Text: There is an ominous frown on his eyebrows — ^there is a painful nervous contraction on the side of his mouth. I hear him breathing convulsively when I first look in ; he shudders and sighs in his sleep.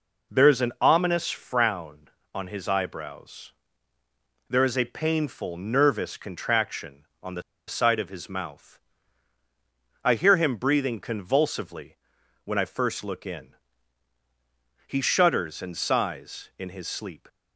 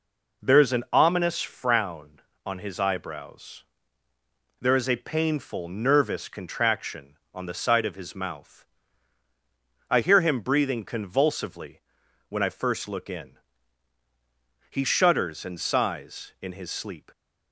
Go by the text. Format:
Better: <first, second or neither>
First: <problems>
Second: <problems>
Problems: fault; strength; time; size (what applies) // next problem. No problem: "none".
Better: second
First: pauses between "the" and "side"; slight; at 7.4 s; 0.25 s long // pauses between "convulsively" and "when"; noticeable; at 11.9 s; 0.48 s long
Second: pauses between "convulsively" and "when"; noticeable; at 11.8 s; 0.48 s long